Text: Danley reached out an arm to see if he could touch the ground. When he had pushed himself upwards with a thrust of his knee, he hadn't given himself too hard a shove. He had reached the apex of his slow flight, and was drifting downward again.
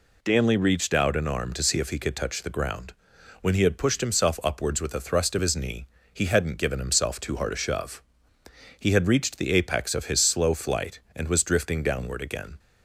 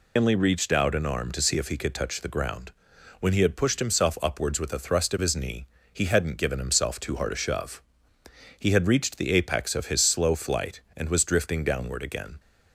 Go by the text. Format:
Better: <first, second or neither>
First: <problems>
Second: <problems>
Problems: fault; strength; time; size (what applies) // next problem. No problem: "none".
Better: first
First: none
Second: loses the start of "Danley"; at 0.1 s; 145 ms